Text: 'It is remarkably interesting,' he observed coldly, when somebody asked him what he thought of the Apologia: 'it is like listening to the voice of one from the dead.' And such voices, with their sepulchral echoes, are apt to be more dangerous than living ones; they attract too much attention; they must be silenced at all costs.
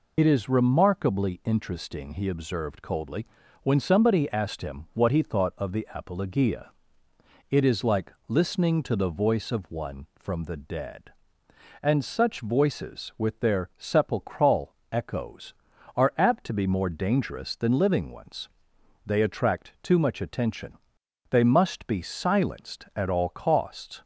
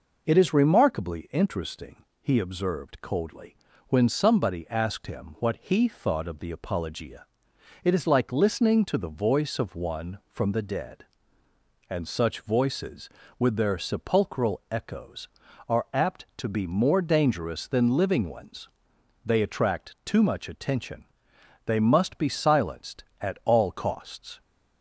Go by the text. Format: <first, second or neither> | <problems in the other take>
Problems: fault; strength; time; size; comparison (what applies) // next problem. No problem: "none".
second | loses the start of "It"; at 0.1 s; 65 ms // pauses between "like" and "listening"; slight; at 8.1 s; 0.16 s long // pauses between "sepulchral" and "echoes"; slight; at 14.7 s; 0.18 s long